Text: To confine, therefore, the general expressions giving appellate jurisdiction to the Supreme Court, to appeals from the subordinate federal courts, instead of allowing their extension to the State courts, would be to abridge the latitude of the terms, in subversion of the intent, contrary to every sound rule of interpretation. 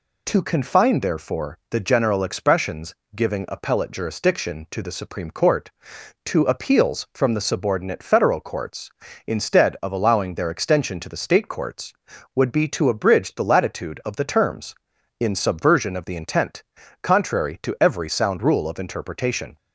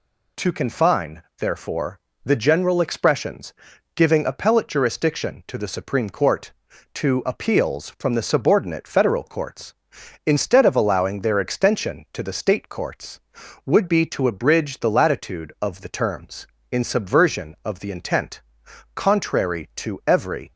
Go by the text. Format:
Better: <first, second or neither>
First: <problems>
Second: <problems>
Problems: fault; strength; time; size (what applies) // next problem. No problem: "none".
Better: first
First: pauses between "expressions" and "giving"; slight; at 2.9 s; 0.18 s long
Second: pauses between "expressions" and "giving"; at 3.5 s; 0.42 s long // stops before "sound rule of interpretation"; at 20.5 s